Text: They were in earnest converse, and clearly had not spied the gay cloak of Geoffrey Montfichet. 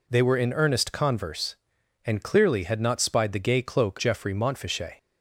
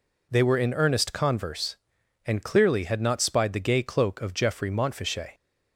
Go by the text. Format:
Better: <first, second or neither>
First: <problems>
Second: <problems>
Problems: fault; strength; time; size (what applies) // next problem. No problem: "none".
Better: second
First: skips "of"; at 3.9 s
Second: none